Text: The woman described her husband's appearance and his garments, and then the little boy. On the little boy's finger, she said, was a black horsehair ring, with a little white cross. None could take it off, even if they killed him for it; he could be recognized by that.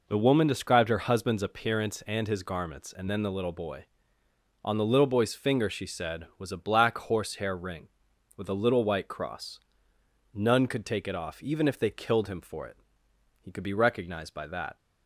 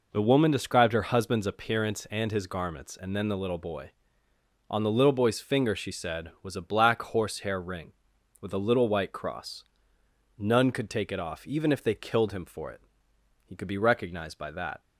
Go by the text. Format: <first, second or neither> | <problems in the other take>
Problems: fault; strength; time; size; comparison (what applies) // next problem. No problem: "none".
neither | none